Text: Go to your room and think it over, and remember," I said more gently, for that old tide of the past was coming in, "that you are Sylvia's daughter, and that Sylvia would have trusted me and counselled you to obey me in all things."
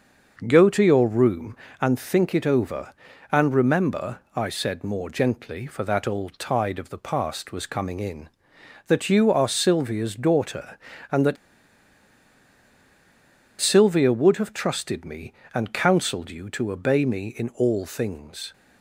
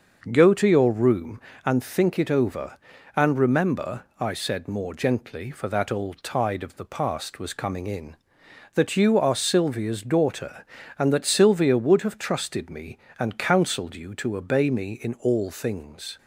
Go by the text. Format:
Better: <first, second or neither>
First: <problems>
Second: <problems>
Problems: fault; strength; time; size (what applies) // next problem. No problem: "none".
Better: second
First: starts louder than the rest; noticeable; until 1.4 s; 6 dB // pauses between "that" and "Sylvia"; strong; at 11.3 s; 2.2 s long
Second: starts louder than the rest; noticeable; until 1.3 s; 6 dB